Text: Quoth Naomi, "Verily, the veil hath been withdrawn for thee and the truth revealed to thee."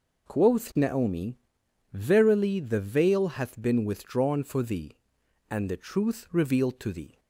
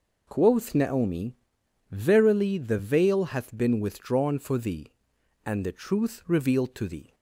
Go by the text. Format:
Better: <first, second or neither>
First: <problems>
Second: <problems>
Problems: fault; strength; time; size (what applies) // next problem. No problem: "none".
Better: neither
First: none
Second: none